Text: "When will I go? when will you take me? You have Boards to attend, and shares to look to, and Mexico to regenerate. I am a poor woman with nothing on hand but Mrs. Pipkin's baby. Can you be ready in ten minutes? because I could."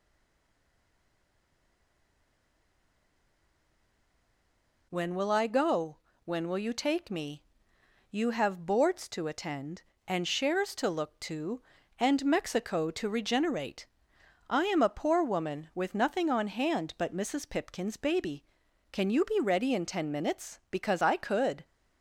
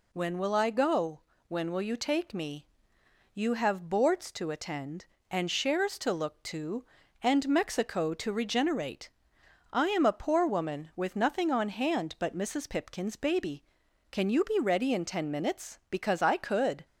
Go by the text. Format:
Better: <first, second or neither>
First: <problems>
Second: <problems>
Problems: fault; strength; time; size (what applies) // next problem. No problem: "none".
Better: second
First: stays silent before the first word; strong; until 4.8 s; 4.8 s long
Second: none